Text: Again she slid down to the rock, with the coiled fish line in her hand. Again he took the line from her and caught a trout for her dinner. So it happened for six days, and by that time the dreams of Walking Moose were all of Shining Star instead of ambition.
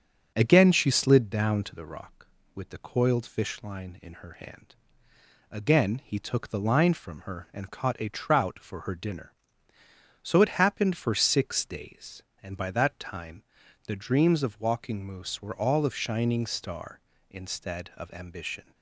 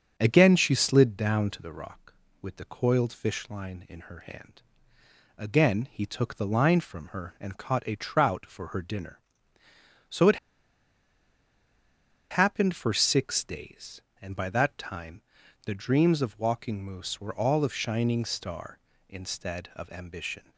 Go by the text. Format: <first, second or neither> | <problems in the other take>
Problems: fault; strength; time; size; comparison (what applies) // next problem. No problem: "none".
first | starts louder than the rest; until 1.1 s; 7 dB; also in the first // pauses between "it" and "happened"; strong; at 10.3 s; 1.9 s long // pauses between "time" and "the"; at 15.2 s; 0.44 s long; also in the first